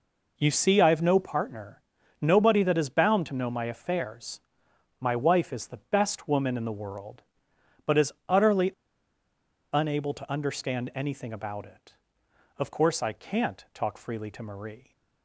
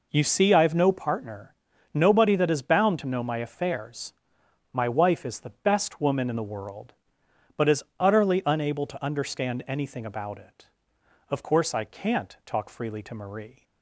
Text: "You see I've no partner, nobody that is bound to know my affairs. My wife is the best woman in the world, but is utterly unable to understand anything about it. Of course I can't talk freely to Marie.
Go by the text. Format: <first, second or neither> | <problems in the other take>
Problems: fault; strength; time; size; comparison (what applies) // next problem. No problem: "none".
second | pauses between "is" and "utterly"; slight; at 8.1 s; 0.16 s long; slight in the second // pauses between "utterly" and "unable"; at 8.6 s; 1.0 s long